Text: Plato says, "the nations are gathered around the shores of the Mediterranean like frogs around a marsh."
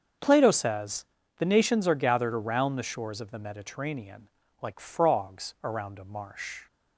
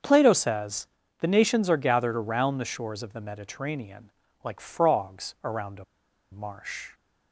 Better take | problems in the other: first | starts louder than the rest; until 1.3 s; 6.5 dB; also in the first // pauses between "Mediterranean" and "like"; slight; at 4.0 s; 0.34 s long; slight in the first // pauses between "a" and "marsh"; noticeable; at 5.8 s; 0.47 s long

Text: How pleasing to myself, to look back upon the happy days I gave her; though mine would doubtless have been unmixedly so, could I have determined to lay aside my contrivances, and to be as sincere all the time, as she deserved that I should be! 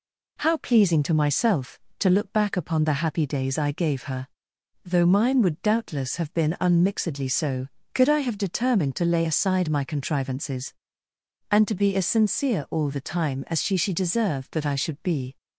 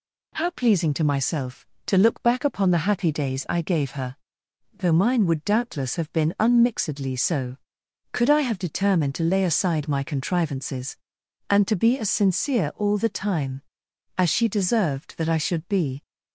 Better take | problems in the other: second | says "she" twice; at 13.7 s

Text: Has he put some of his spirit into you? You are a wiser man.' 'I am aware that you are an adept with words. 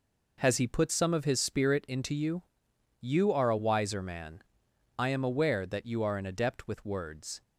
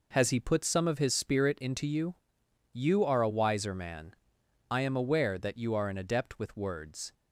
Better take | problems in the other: neither | none

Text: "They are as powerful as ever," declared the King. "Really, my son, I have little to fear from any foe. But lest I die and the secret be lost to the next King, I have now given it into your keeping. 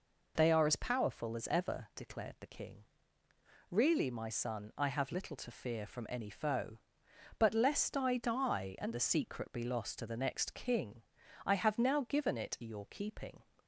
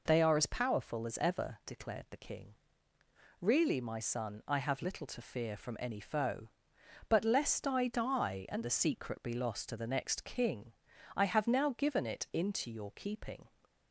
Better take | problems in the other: second | skips "into"; at 12.6 s

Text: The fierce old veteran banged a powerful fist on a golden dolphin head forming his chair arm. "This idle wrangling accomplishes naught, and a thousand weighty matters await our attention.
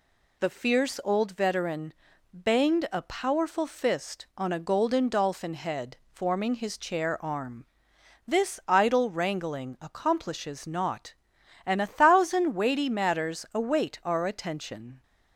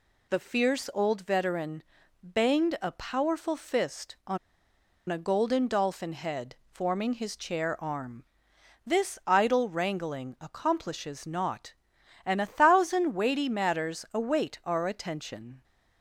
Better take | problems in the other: first | pauses between "veteran" and "banged"; at 1.8 s; 0.40 s long; also in the first // pauses between "on" and "a"; noticeable; at 4.3 s; 0.71 s long

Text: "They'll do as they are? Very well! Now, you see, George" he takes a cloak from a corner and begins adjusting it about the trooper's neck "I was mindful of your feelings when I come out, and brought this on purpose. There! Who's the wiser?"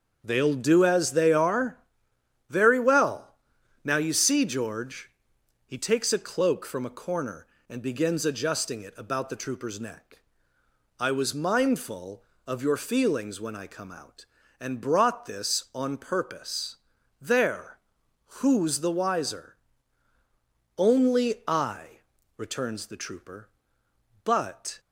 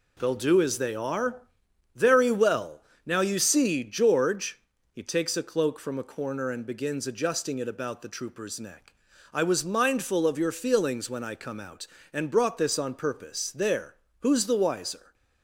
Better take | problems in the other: second | starts louder than the rest; until 1.2 s; 6.5 dB // pauses between "George" and "he"; noticeable; at 5.0 s; 0.58 s long; slight in the second // pauses between "neck" and "I"; noticeable; at 10.2 s; 0.76 s long; also in the second // goes on to say "Only I returns the trooper but"; strong; from 20.7 s on; 4.0 s long

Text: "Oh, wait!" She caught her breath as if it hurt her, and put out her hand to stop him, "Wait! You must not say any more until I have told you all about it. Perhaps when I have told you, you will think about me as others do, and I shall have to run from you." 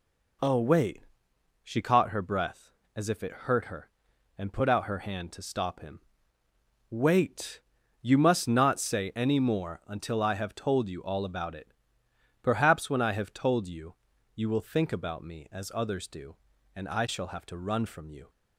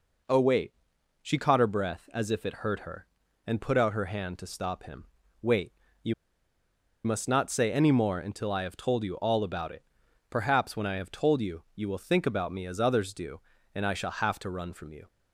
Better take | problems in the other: first | pauses between "You" and "must"; noticeable; at 6.1 s; 0.90 s long

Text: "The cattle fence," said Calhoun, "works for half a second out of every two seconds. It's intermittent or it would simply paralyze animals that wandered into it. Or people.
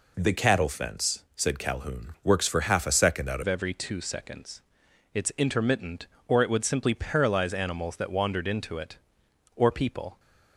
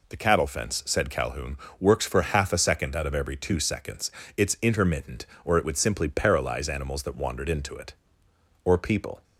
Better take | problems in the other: second | changes voice at "of"; from 3.4 s on; 6.7 s long

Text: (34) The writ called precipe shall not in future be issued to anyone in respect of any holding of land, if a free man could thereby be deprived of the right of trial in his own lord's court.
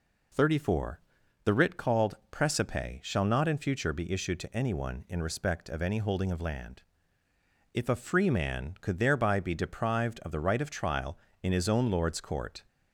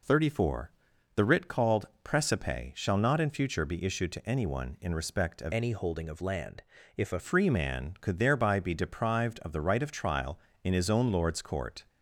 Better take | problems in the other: first | pauses between "called" and "precipe"; slight; at 1.8 s; 0.16 s long // changes voice from "any" to "a"; from 5.5 to 7.1 s; 1.6 s long

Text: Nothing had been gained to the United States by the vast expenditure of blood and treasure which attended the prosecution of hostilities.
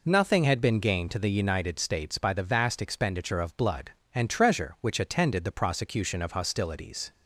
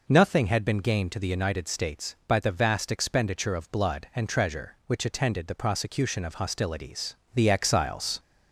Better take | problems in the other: first | goes on to say "The Exiles"; noticeable; from 7.3 s on; 0.84 s long

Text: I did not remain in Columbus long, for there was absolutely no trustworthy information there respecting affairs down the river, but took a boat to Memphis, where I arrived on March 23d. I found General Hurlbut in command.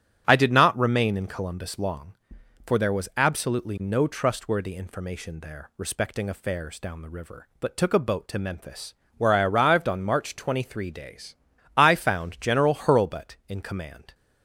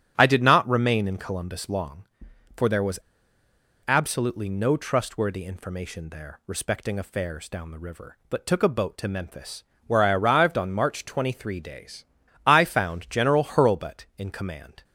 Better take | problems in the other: first | starts louder than the rest; strong; until 1.1 s; 10 dB; strong in the first // pauses between "was" and "absolutely"; noticeable; at 2.9 s; 0.86 s long

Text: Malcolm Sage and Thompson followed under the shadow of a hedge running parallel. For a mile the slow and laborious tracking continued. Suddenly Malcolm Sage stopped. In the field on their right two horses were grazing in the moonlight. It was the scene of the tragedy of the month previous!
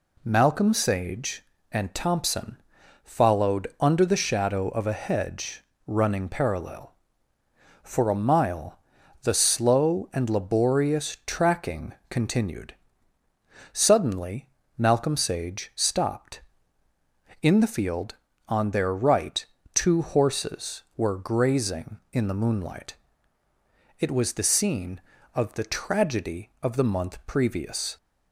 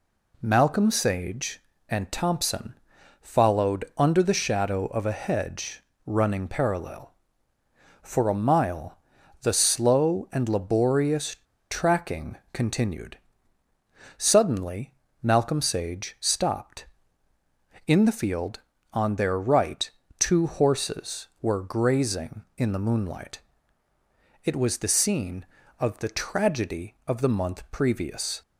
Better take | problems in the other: first | pauses between "Thompson" and "followed"; noticeable; at 2.7 s; 0.48 s long; noticeable in the first // pauses between "hedge" and "running"; slight; at 5.8 s; 0.24 s long; slight in the first // pauses between "mile" and "the"; noticeable; at 8.9 s; 0.46 s long; noticeable in the first // pauses between "laborious" and "tracking"; slight; at 11.3 s; 0.32 s long // pauses between "tracking" and "continued"; slight; at 12.3 s; 0.16 s long; slight in the first // pauses between "Suddenly" and "Malcolm"; slight; at 14.9 s; 0.30 s long; slight in the first // pauses between "right" and "two"; slight; at 19.8 s; 0.28 s long; slight in the first

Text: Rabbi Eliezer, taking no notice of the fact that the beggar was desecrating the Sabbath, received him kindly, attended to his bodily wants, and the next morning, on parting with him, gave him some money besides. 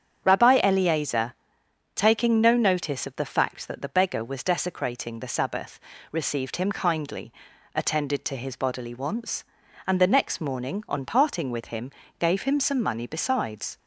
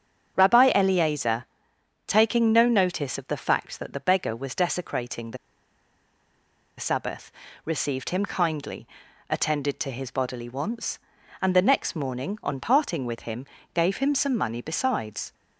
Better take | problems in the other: first | starts louder than the rest; strong; until 1.3 s; 7.5 dB; strong in the first // pauses between "the" and "Sabbath"; strong; at 5.3 s; 1.4 s long

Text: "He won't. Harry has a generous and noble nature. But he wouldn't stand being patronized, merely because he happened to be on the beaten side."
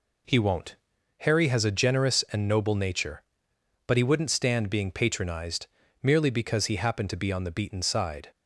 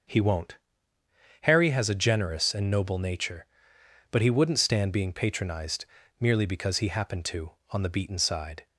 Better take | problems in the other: first | starts louder than the rest; noticeable; until 1.9 s; 6 dB // skips "be"; at 7.6 s

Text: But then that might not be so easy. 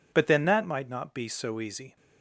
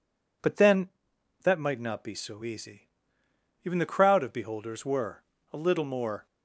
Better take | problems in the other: first | goes on to say "Even the crowd of beholders were a little more"; strong; from 3.6 s on; 2.6 s long

